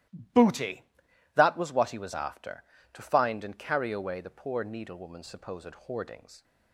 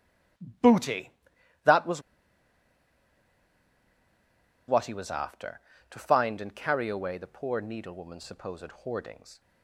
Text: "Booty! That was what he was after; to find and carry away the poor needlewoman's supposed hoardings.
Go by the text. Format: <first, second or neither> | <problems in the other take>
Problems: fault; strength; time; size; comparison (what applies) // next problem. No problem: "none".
first | starts louder than the rest; strong; until 1.9 s; 14 dB; strong in the first // pauses between "was" and "what"; strong; at 2.0 s; 2.6 s long